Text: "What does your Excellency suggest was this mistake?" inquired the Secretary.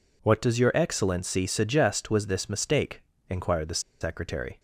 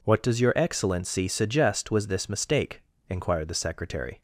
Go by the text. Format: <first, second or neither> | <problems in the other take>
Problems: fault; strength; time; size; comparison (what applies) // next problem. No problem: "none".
second | pauses between "the" and "Secretary"; slight; at 3.7 s; 0.21 s long